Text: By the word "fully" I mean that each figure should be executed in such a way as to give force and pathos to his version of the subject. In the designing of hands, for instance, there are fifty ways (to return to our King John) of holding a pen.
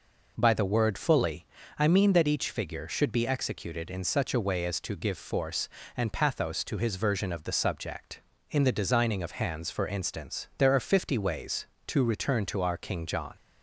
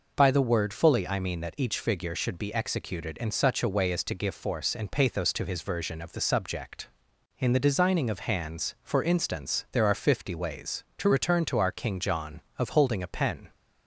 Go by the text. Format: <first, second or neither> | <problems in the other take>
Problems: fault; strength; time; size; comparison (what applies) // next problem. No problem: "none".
second | pauses between "fully" and "I"; slight; at 1.4 s; 0.34 s long // stops before "of holding a pen"; at 13.3 s